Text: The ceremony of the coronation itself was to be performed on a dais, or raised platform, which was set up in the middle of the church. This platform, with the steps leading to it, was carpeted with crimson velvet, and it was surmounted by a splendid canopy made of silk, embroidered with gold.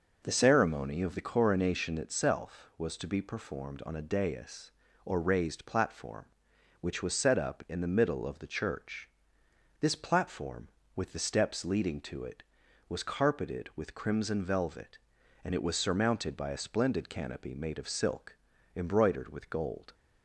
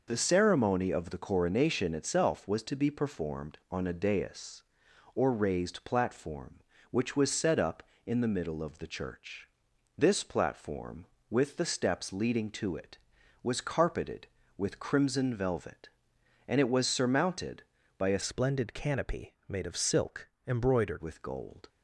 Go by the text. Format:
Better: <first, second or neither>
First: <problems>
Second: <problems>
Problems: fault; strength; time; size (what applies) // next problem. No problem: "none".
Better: first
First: none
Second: changes voice from "splendid" to "embroidered"; from 18.2 to 21.0 s; 2.8 s long